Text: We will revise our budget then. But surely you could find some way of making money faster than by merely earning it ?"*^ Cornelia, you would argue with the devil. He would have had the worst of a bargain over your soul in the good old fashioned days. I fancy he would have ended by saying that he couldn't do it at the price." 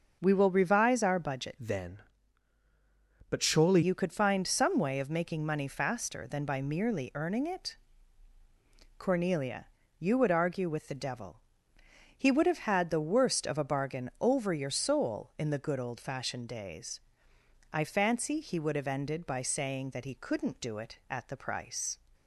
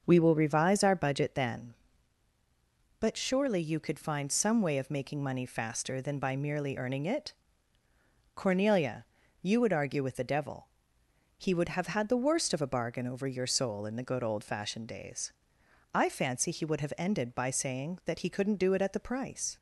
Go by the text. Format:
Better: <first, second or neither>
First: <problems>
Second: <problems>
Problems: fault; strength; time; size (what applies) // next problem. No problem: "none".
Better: second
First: starts louder than the rest; until 1.2 s; 6.5 dB // changes voice from "then" to "surely"; from 1.5 to 3.8 s; 2.3 s long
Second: starts louder than the rest; until 1.0 s; 6.5 dB